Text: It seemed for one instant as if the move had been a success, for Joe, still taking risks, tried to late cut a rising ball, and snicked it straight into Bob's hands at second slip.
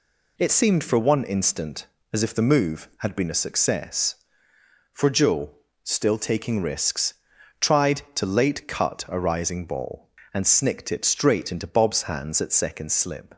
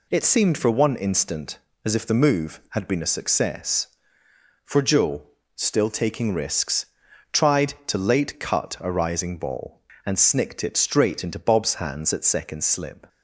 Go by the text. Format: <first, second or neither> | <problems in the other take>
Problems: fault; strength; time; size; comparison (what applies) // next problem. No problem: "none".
neither | none